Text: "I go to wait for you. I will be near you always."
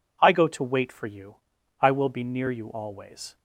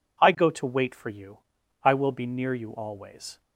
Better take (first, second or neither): neither